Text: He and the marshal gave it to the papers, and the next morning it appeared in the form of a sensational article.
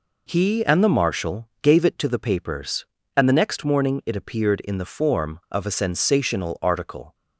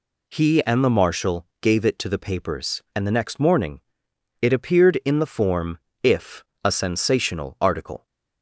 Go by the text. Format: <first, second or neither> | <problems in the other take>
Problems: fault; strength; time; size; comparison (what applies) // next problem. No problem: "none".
first | pauses between "marshal" and "gave"; slight; at 1.4 s; 0.16 s long // pauses between "morning" and "it"; noticeable; at 3.7 s; 0.62 s long // says "if" for "of"; at 6.0 s